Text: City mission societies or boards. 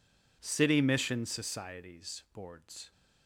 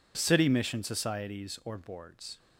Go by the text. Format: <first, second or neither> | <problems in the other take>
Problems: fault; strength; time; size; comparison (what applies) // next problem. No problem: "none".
second | skips "or"; at 2.2 s